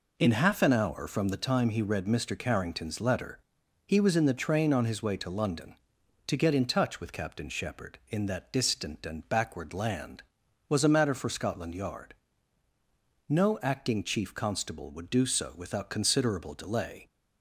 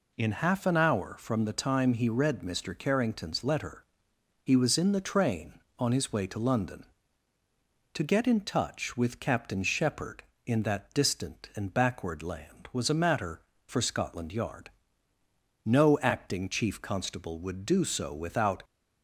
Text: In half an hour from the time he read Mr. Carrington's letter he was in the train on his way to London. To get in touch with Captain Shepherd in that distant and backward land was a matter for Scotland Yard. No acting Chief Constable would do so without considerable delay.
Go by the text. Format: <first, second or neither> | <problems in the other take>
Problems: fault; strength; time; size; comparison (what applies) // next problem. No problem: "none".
first | pauses between "letter" and "he"; noticeable; at 3.8 s; 0.60 s long; noticeable in the first // stops before "considerable delay"; at 18.6 s